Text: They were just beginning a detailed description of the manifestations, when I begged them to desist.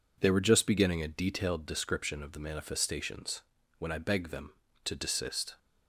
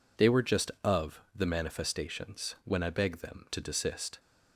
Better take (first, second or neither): first